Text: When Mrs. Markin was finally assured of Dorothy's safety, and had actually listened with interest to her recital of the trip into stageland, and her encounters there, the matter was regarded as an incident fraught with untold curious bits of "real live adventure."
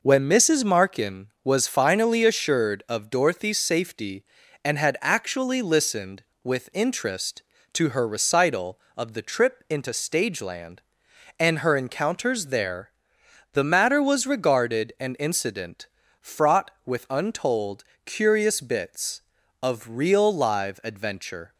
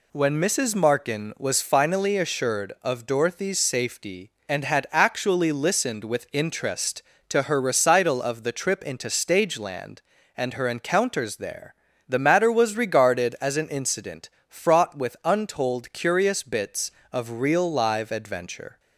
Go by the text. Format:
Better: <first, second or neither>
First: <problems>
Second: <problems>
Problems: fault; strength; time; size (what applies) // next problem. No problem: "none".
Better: second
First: skips "as"; at 14.9 s // pauses between "incident" and "fraught"; slight; at 15.8 s; 0.34 s long // pauses between "untold" and "curious"; slight; at 17.8 s; 0.20 s long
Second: pauses between "incident" and "fraught"; slight; at 14.2 s; 0.18 s long